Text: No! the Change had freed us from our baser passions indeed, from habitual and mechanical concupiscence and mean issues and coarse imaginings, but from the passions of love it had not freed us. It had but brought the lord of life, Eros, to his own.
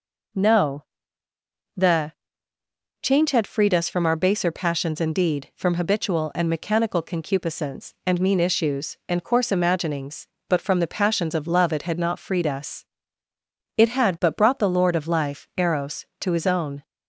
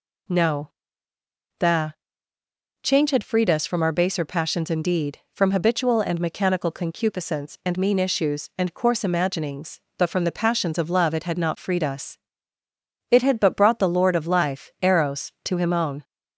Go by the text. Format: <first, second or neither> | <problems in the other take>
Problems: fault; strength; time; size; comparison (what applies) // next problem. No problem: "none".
first | pauses between "the" and "Change"; noticeable; at 1.9 s; 0.88 s long; noticeable in the first // says "him" for "his"; at 15.5 s